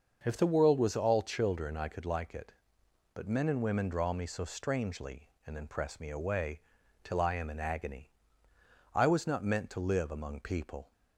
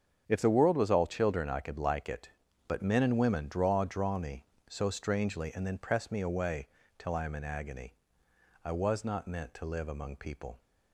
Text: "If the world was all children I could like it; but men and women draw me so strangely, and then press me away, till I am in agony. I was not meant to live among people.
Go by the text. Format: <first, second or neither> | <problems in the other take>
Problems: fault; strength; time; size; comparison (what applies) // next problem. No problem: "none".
first | starts louder than the rest; strong; until 1.2 s; 7.5 dB; also in the first // says "draw" twice; at 3.8 s